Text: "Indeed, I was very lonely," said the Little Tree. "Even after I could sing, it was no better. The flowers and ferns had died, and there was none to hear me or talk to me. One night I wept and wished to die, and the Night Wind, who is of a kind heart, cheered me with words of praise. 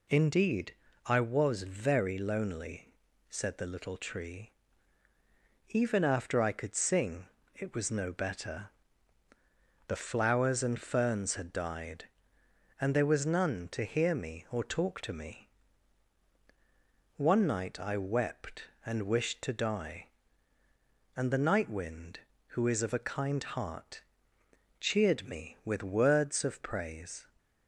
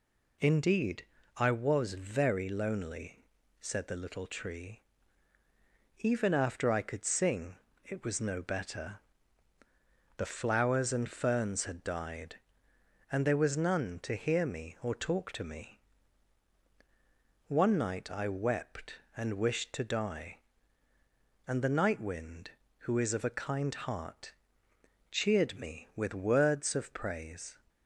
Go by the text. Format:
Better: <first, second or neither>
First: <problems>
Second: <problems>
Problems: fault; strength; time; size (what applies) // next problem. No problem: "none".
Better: neither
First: none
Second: none